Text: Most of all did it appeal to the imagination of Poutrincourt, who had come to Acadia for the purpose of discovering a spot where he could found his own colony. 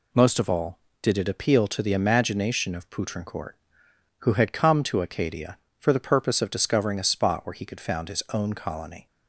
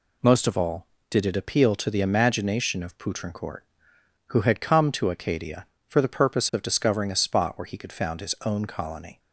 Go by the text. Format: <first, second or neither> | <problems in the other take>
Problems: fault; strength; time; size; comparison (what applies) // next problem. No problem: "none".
neither | none